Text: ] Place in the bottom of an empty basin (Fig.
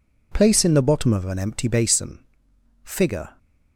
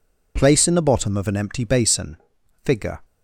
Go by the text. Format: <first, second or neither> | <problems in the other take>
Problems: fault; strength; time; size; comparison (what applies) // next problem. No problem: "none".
neither | none